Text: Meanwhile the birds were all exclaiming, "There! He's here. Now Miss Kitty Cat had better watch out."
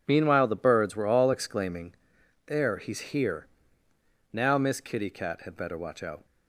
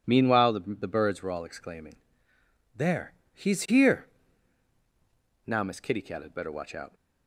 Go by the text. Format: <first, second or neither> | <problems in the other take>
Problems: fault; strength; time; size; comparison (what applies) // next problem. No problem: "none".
first | says "the" twice; at 0.7 s